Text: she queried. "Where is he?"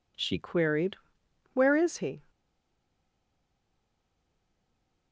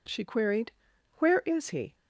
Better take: second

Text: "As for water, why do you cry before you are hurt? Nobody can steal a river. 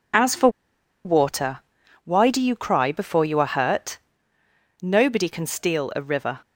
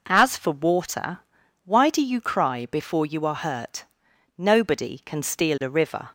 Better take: second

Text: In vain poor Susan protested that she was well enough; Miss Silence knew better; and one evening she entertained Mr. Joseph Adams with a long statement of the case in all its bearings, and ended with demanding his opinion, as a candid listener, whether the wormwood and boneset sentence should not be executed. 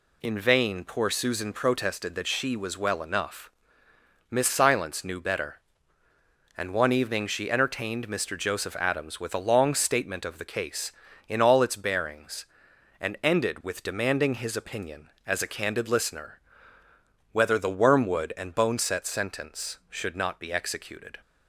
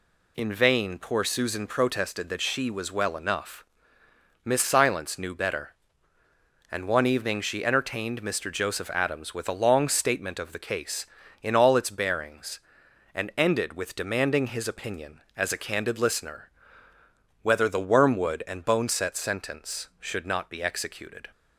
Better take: neither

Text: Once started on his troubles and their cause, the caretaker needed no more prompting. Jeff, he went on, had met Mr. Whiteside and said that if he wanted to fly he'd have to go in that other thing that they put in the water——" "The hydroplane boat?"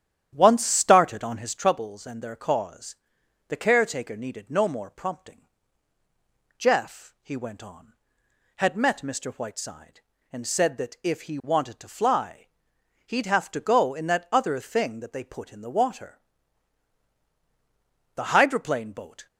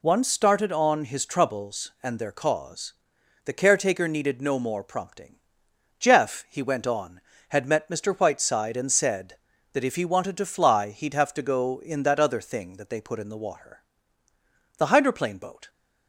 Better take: second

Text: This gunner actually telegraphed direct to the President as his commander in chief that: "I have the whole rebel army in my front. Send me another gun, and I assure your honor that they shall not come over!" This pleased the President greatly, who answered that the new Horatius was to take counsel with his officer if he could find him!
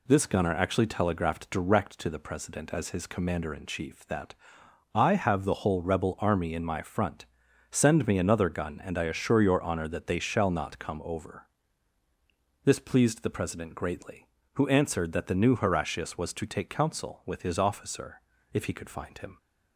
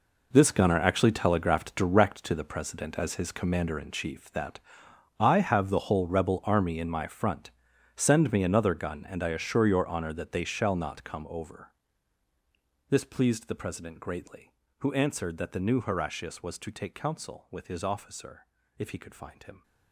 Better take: first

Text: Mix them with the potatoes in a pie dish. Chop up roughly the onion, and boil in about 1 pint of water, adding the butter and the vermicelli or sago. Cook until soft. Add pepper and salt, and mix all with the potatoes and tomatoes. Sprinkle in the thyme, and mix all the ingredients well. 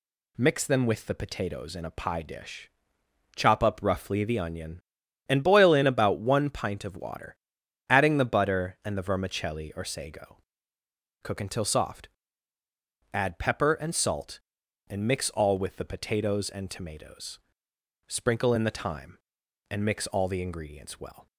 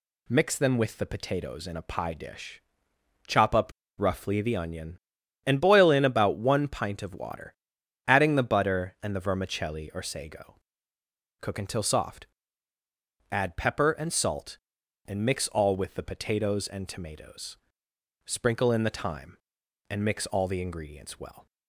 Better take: first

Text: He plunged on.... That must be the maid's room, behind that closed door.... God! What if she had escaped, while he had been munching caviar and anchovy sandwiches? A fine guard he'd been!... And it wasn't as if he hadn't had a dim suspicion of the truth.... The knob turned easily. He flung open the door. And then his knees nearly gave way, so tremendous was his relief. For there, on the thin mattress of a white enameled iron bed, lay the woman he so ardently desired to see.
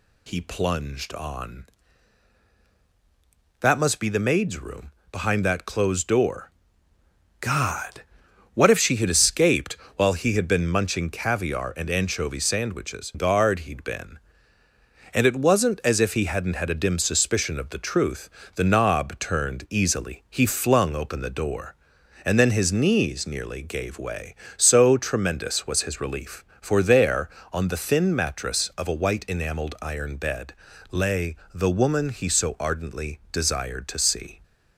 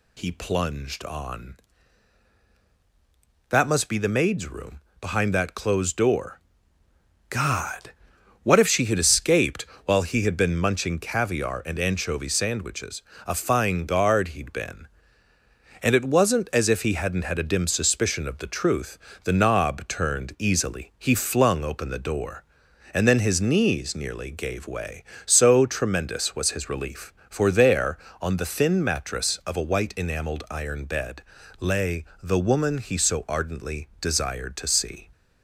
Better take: second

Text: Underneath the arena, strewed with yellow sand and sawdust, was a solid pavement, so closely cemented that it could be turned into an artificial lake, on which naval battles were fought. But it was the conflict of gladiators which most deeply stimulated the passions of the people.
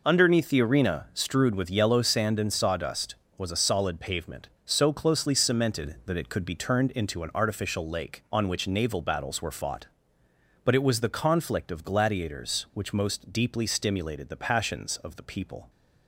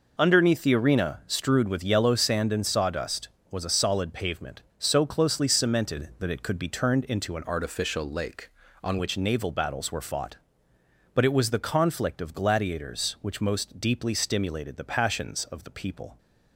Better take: first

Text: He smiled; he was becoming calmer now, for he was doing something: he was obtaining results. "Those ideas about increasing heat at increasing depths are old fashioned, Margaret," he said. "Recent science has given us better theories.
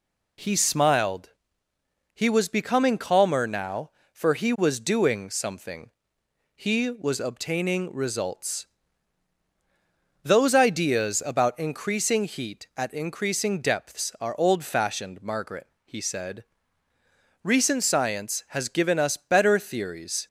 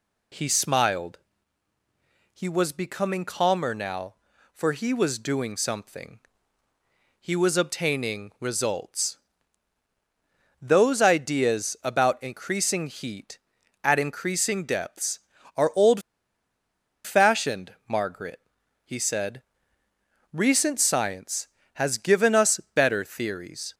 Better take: first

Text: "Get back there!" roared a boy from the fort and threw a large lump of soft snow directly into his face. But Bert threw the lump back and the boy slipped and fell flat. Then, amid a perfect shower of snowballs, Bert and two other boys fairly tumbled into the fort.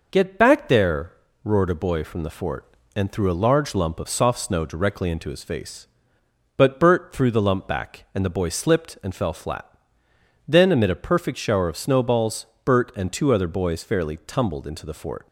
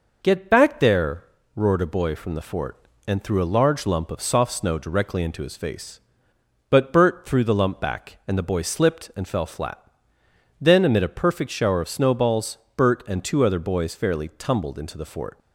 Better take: neither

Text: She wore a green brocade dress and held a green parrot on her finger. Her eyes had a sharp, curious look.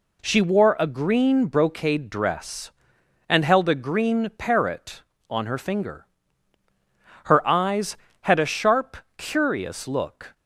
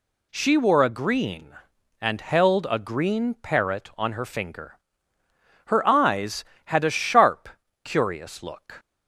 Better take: first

